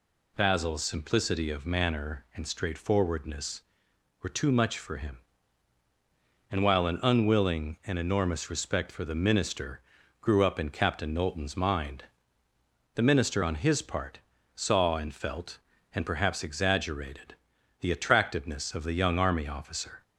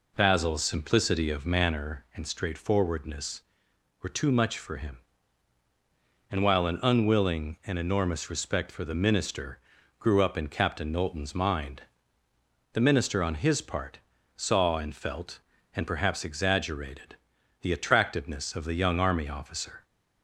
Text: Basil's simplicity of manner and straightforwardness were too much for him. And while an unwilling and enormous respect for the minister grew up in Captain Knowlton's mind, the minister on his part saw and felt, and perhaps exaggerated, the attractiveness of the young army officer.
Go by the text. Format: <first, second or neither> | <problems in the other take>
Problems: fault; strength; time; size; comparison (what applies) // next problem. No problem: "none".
first | starts louder than the rest; until 1.9 s; 3.5 dB // pauses between "minister" and "grew"; at 9.5 s; 0.40 s long; also in the first // pauses between "part" and "saw"; slight; at 13.9 s; 0.36 s long; slight in the first